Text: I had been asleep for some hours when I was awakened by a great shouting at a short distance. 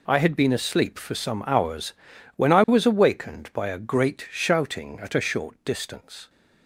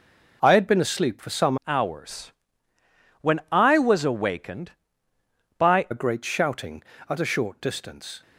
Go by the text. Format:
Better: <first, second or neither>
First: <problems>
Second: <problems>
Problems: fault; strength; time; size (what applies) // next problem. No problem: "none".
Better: first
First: pauses between "hours" and "when"; at 1.9 s; 0.42 s long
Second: changes voice from "hours" to "by"; from 1.6 to 5.8 s; 4.2 s long // pauses between "hours" and "when"; noticeable; at 2.3 s; 0.88 s long